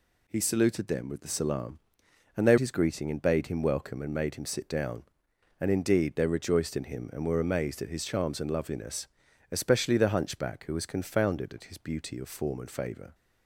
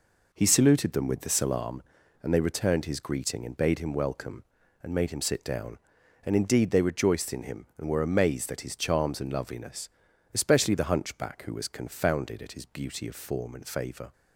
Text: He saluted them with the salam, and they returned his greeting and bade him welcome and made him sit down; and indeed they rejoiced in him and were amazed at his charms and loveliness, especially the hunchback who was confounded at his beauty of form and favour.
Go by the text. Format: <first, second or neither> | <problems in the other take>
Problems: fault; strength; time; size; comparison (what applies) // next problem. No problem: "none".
second | skips "returned"; at 2.5 s